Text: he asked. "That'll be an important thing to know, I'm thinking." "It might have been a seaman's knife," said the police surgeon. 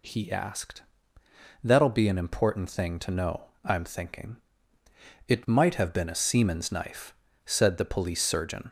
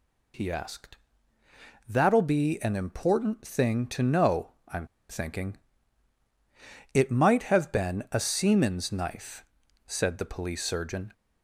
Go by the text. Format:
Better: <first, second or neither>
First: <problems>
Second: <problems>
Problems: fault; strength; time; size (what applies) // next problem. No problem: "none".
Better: first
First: none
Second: pauses between "I'm" and "thinking"; slight; at 4.8 s; 0.24 s long